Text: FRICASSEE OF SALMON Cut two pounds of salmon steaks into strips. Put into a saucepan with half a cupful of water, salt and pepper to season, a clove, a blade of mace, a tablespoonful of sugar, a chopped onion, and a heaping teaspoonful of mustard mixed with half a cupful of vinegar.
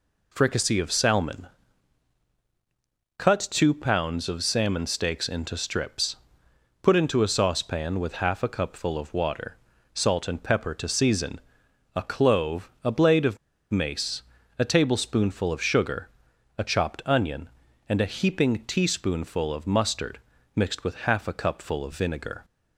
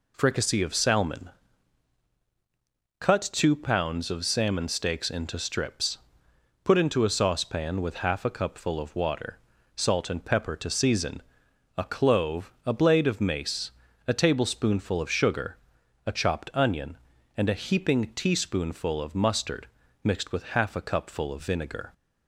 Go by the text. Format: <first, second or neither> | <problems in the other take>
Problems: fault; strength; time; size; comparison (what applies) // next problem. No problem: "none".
second | pauses between "SALMON" and "Cut"; strong; at 1.4 s; 1.7 s long; strong in the second // pauses between "of" and "mace"; slight; at 13.3 s; 0.33 s long // pauses between "mustard" and "mixed"; slight; at 20.2 s; 0.34 s long; slight in the second